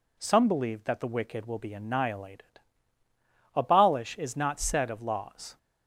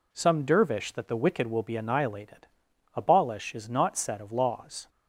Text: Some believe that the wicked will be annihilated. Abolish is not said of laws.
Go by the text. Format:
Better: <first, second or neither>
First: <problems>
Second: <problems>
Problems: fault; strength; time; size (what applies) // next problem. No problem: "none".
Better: first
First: none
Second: says "dervish" for "believe"; at 0.4 s